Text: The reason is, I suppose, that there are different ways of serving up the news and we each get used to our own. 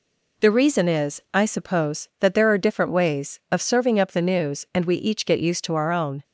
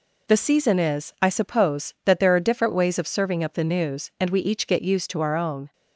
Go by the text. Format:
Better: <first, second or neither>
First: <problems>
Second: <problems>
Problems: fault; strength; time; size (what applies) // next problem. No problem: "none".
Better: first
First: none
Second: says "season" for "reason"; at 0.3 s